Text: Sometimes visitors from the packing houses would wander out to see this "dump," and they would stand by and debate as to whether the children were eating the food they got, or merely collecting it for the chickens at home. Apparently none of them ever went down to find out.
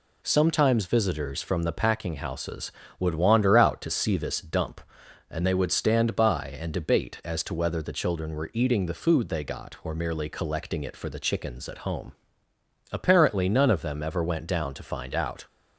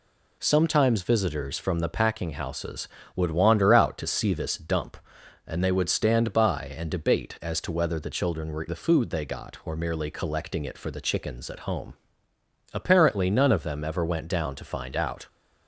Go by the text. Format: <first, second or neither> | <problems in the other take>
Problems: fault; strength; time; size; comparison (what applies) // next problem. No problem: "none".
first | skips "eating"; at 8.6 s